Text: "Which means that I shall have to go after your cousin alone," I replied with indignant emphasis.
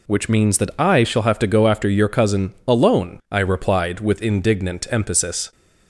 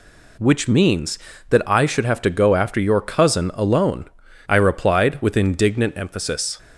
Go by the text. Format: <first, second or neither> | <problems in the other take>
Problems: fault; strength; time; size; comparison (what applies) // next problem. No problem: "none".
first | says "should" for "shall"; at 1.8 s